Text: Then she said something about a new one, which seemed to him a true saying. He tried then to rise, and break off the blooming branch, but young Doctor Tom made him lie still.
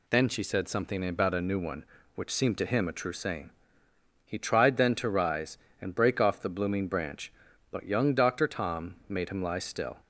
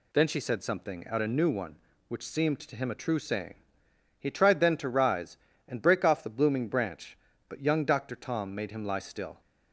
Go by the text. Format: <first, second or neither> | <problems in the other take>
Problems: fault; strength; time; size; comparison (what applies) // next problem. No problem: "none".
first | says "out" for "about"; at 1.0 s